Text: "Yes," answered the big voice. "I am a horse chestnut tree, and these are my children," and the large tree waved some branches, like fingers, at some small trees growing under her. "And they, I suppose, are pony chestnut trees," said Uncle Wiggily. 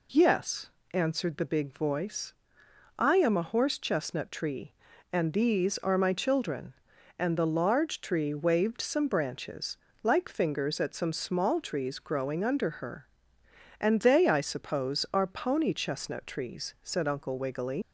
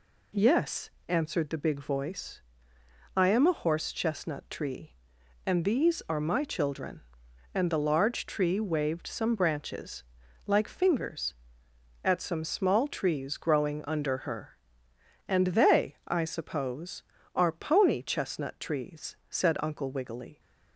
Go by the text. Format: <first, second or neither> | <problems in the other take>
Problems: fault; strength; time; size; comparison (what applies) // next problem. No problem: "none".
second | leaves "Wiggily" unfinished; at 17.8 s; 105 ms